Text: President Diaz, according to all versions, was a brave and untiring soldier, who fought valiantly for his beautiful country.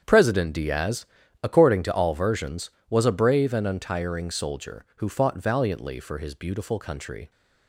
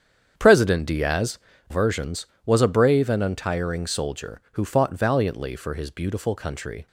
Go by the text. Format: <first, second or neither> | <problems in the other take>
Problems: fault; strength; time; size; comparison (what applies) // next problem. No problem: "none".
first | starts louder than the rest; strong; until 1.3 s; 8 dB; strong in the first // skips "according to all"; at 1.5 s